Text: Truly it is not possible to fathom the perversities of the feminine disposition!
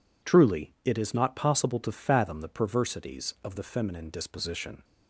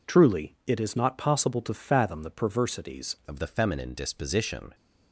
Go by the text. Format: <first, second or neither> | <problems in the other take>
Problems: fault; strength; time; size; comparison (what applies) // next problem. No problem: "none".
first | changes voice at "of"; from 3.2 s on; 1.5 s long